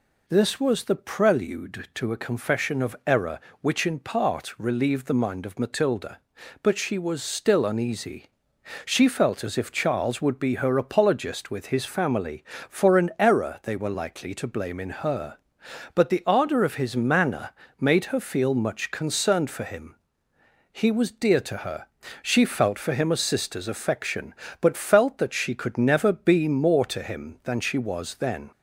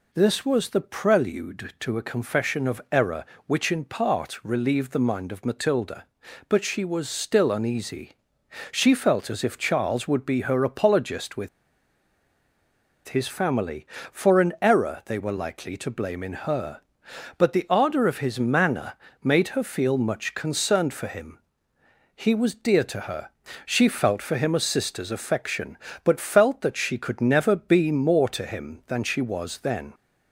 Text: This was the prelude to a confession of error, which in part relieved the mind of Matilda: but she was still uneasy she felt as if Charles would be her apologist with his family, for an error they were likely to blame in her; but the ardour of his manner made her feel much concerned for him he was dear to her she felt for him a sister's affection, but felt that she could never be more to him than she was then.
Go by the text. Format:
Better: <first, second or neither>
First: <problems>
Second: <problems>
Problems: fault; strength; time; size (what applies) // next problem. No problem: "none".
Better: first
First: pauses between "uneasy" and "she"; noticeable; at 8.2 s; 0.60 s long // pauses between "manner" and "made"; slight; at 17.5 s; 0.30 s long // pauses between "him" and "he"; noticeable; at 19.9 s; 0.74 s long // pauses between "her" and "she"; slight; at 21.8 s; 0.34 s long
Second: pauses between "uneasy" and "she"; noticeable; at 8.1 s; 0.60 s long // pauses between "with" and "his"; strong; at 11.4 s; 1.5 s long // pauses between "manner" and "made"; slight; at 18.9 s; 0.30 s long // pauses between "him" and "he"; noticeable; at 21.4 s; 0.74 s long // pauses between "her" and "she"; slight; at 23.3 s; 0.34 s long